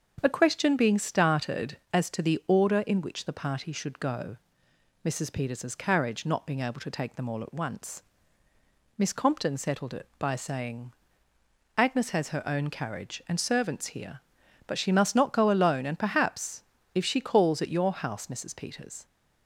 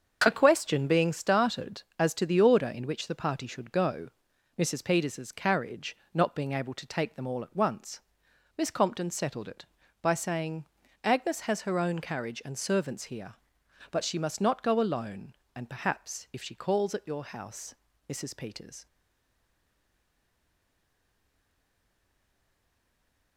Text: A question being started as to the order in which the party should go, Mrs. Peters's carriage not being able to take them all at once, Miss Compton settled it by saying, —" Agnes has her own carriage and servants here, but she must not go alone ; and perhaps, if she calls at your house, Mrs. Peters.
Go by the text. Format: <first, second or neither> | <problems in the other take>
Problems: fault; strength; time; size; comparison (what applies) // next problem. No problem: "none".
first | starts louder than the rest; until 1.2 s; 7 dB; also in the first // pauses between "carriage" and "not"; slight; at 5.9 s; 0.18 s long // stays silent after the last word; strong; from 18.8 s on; 4.5 s long